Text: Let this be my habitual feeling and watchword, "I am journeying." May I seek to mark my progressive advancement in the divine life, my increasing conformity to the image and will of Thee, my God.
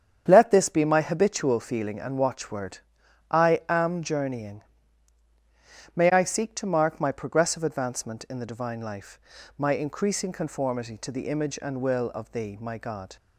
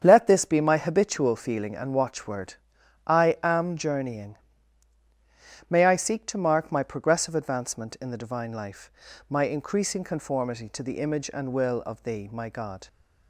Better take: neither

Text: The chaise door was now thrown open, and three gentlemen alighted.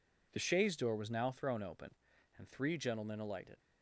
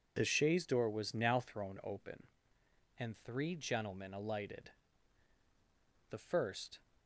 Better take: first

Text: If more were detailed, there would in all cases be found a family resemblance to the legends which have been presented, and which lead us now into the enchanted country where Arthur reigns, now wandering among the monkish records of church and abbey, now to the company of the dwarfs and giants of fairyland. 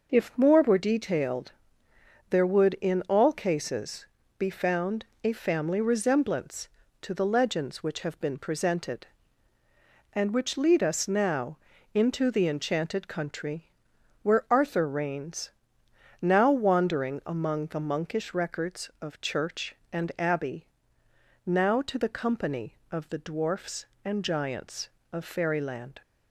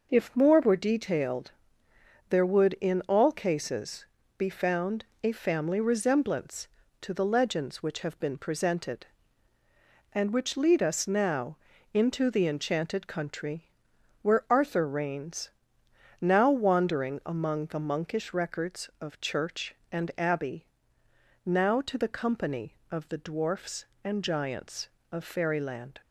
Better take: neither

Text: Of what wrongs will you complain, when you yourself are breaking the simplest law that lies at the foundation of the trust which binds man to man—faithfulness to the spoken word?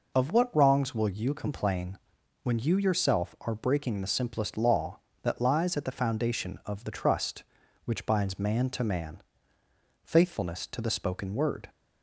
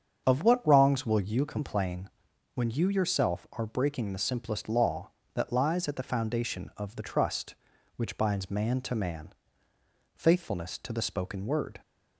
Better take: first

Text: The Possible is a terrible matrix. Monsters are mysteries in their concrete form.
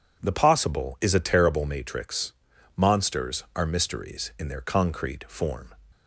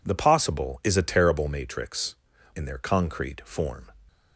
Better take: first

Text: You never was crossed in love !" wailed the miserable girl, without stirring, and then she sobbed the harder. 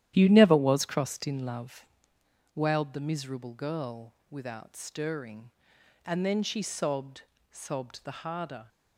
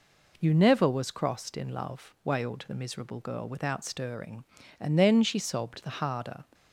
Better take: second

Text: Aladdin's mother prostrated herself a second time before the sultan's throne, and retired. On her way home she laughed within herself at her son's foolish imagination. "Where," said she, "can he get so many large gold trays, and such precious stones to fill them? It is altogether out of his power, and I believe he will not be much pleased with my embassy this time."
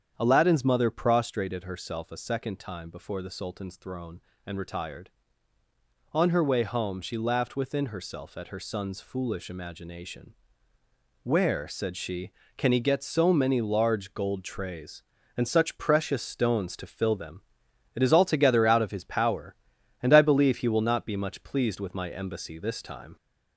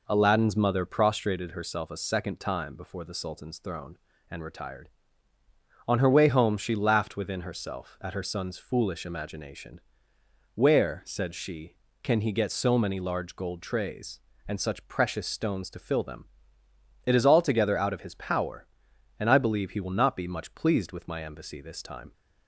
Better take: second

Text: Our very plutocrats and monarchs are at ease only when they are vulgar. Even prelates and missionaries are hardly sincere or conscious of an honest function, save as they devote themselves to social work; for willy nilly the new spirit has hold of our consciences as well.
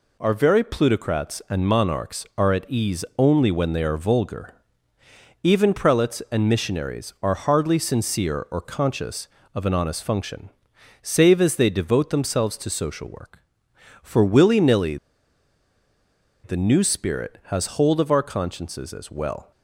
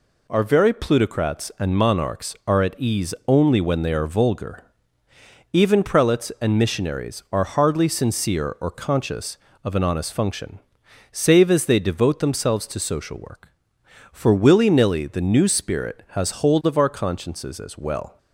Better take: second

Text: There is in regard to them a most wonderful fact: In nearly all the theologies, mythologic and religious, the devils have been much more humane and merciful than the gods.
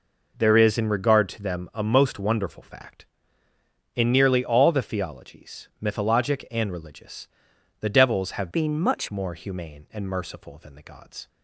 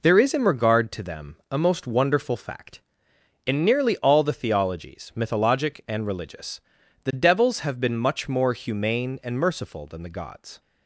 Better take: second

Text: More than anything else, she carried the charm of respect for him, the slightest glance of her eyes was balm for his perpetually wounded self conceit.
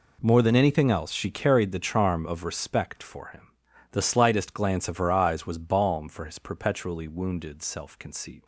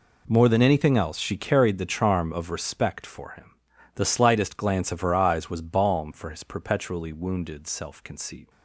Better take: neither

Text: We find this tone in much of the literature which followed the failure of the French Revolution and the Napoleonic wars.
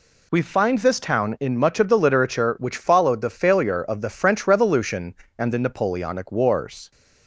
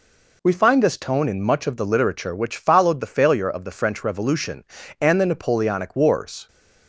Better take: second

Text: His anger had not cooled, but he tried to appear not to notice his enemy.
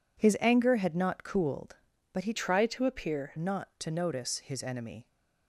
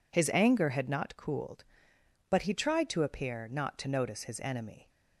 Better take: second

